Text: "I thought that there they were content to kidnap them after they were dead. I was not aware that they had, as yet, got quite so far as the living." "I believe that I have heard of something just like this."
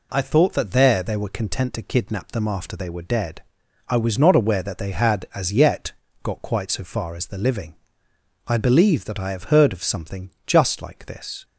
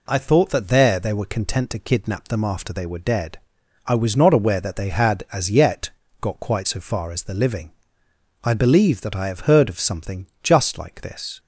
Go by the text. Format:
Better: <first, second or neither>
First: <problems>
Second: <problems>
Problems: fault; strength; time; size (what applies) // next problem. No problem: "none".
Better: neither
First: pauses between "something" and "just"; slight; at 10.3 s; 0.16 s long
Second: pauses between "something" and "just"; slight; at 10.2 s; 0.16 s long